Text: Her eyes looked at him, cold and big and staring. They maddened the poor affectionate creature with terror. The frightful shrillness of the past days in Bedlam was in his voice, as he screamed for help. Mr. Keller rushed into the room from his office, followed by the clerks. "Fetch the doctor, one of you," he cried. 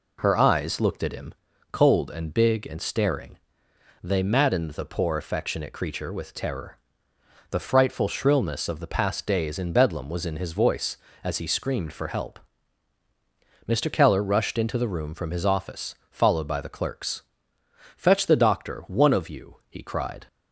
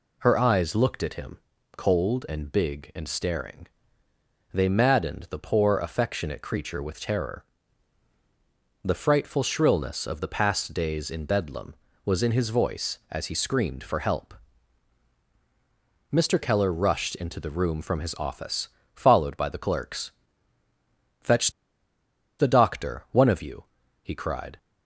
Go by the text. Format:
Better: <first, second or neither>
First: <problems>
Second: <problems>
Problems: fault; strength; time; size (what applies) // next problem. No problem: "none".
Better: first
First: none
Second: pauses between "Fetch" and "the"; noticeable; at 21.5 s; 0.88 s long